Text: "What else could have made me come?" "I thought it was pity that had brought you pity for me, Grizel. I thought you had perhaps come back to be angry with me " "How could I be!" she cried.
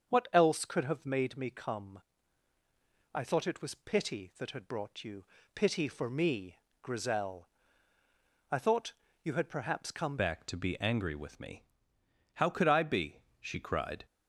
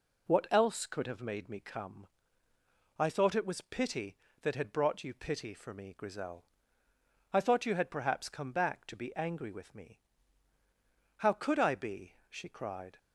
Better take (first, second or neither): second